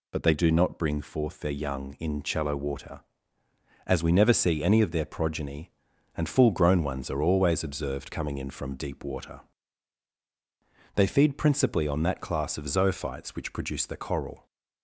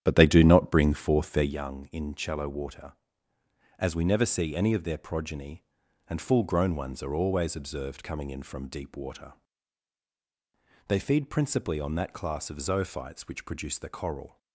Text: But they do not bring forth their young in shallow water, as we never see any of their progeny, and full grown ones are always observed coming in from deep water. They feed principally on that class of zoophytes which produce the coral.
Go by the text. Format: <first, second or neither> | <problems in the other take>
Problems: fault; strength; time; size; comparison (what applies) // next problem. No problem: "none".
first | starts louder than the rest; strong; until 1.5 s; 10 dB